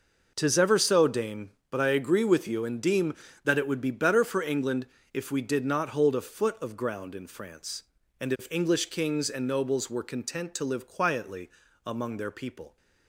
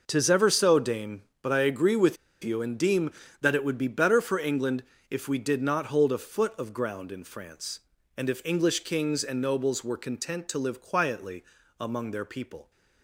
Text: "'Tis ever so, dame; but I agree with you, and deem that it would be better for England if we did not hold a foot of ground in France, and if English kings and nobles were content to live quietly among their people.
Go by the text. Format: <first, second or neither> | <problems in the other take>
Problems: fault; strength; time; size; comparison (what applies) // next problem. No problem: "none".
first | pauses between "with" and "you"; slight; at 2.1 s; 0.27 s long // pauses between "England" and "if"; slight; at 4.8 s; 0.26 s long; slight in the first // pauses between "quietly" and "among"; at 11.4 s; 0.38 s long; also in the first